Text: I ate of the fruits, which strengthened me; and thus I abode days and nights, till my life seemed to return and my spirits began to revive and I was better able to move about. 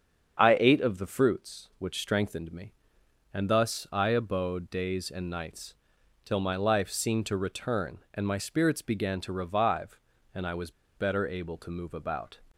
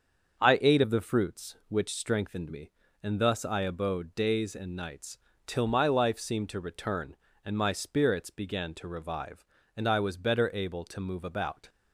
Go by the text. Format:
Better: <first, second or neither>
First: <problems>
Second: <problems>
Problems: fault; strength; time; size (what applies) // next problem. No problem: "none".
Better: second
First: starts louder than the rest; strong; until 1.4 s; 7 dB // pauses between "was" and "better"; slight; at 10.7 s; 0.25 s long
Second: starts louder than the rest; until 1.4 s; 6.5 dB